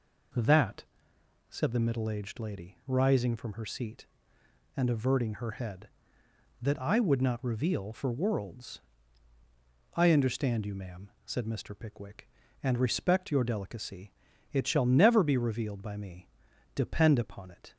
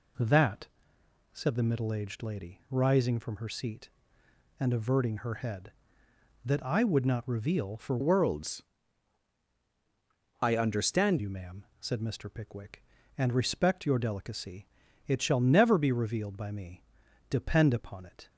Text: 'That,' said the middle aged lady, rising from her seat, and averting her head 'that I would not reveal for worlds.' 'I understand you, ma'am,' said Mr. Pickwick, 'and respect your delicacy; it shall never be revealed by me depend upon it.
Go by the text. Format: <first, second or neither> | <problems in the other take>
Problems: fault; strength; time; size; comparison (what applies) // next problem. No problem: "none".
first | changes voice from "worlds" to "understand"; from 8.0 to 11.1 s; 3.1 s long // pauses between "me" and "depend"; noticeable; at 16.8 s; 0.46 s long; noticeable in the first